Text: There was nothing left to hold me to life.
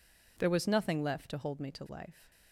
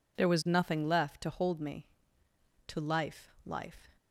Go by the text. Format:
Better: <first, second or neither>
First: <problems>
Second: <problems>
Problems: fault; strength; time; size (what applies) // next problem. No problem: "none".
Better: first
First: none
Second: says "life" twice; at 3.4 s